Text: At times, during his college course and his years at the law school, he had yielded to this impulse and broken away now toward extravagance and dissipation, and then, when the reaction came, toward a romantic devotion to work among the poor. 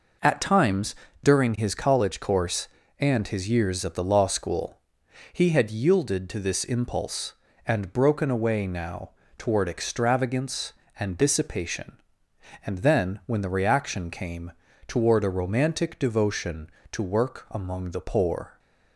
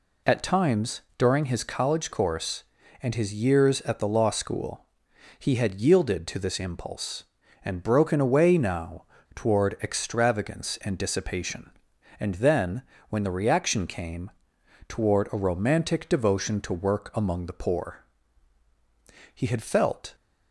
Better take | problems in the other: first | pauses between "now" and "toward"; slight; at 9.0 s; 0.30 s long; slight in the first // goes on to say "He had felt"; noticeable; from 19.3 s on; 0.82 s long

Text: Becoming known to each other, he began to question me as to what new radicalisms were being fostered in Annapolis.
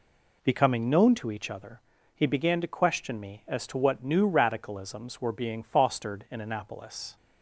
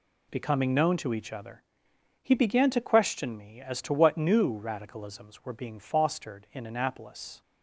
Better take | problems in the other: neither | none

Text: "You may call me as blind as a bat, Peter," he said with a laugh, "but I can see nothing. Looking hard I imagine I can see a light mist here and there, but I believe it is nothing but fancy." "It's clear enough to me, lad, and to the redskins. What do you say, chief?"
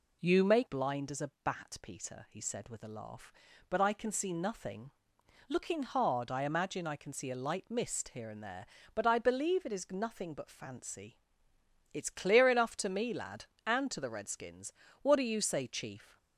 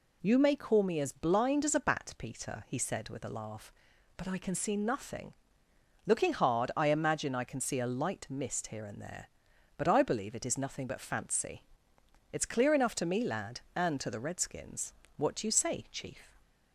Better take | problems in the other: second | skips "call me as"; at 0.6 s

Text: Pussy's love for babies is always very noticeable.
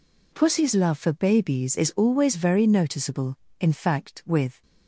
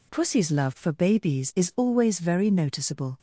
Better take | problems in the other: second | goes on to say "In fact with"; noticeable; from 3.5 s on; 1.0 s long

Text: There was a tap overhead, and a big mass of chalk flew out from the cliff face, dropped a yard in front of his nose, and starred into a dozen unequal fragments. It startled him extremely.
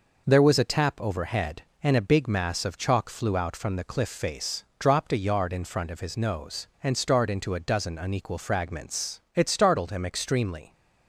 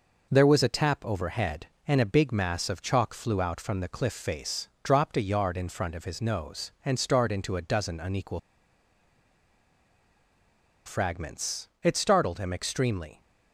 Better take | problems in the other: first | pauses between "unequal" and "fragments"; strong; at 8.3 s; 2.4 s long

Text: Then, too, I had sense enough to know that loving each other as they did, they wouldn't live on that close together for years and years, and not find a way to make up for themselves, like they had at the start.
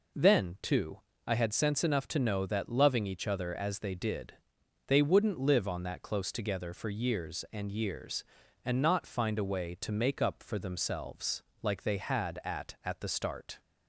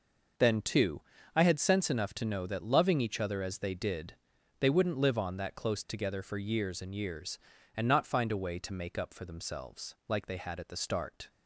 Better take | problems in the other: second | says "at" twice; at 12.8 s

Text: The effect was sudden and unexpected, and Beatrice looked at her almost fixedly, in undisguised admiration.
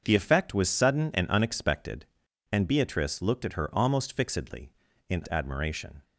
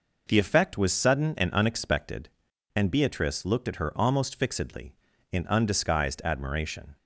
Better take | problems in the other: second | starts louder than the rest; until 1.0 s; 6.5 dB // skips "undisguised"; at 5.2 s

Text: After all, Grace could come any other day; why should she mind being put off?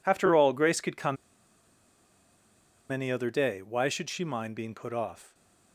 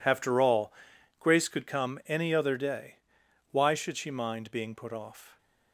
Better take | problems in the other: second | pauses between "come" and "any"; strong; at 1.1 s; 1.7 s long

